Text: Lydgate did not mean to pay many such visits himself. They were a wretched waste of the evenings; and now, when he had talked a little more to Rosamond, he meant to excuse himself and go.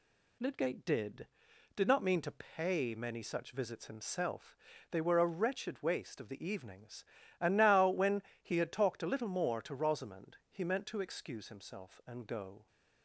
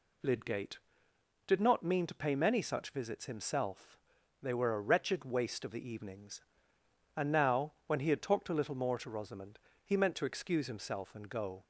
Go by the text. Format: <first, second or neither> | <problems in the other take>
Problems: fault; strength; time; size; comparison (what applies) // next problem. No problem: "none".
second | says "did" twice; at 1.7 s // pauses between "when" and "he"; slight; at 8.2 s; 0.20 s long